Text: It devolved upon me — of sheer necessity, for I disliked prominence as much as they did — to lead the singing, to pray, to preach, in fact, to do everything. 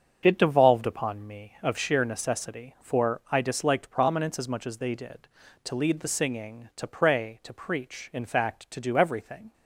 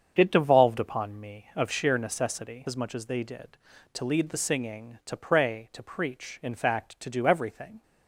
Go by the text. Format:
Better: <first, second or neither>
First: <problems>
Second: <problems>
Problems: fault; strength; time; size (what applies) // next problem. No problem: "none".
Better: first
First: starts louder than the rest; until 1.2 s; 6.5 dB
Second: starts louder than the rest; strong; until 1.1 s; 7.5 dB // skips "for I disliked prominence"; at 2.6 s